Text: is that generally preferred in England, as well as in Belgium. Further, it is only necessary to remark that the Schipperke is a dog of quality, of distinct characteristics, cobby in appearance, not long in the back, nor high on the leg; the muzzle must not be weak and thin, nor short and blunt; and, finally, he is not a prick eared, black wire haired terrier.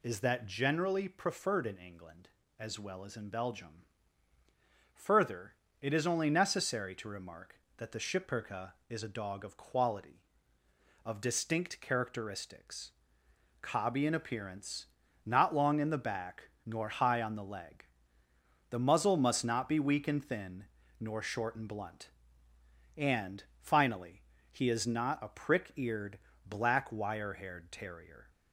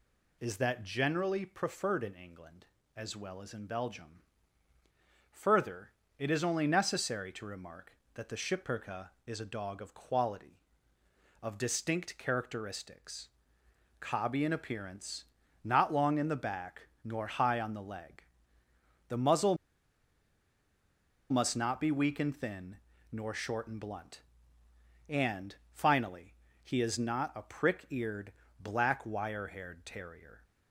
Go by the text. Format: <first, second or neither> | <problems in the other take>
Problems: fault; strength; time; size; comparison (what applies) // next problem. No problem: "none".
first | pauses between "muzzle" and "must"; strong; at 19.5 s; 1.7 s long